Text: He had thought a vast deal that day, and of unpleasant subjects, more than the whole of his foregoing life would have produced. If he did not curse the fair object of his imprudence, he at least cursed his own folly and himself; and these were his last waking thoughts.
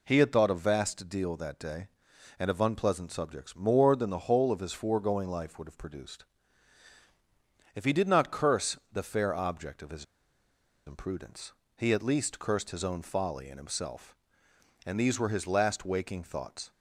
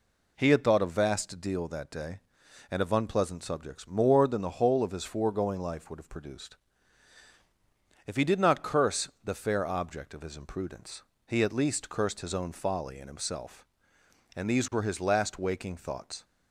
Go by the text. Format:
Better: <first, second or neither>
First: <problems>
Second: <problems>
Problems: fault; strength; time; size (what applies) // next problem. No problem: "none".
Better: second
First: pauses between "curse" and "the"; slight; at 8.7 s; 0.16 s long // pauses between "his" and "imprudence"; noticeable; at 10.0 s; 0.81 s long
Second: pauses between "curse" and "the"; slight; at 9.0 s; 0.16 s long